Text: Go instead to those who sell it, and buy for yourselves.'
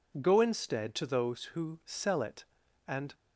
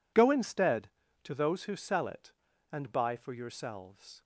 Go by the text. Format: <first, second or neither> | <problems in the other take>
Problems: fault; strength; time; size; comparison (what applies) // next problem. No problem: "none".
second | stops before "buy for yourselves"; at 3.1 s